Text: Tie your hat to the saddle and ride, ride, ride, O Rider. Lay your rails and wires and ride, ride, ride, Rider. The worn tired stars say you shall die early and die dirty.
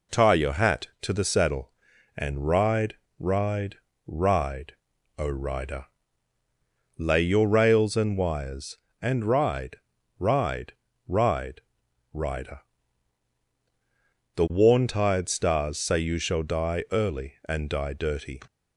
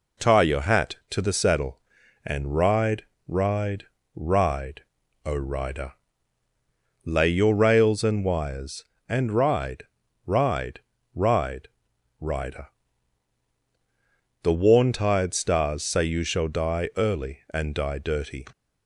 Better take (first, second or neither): neither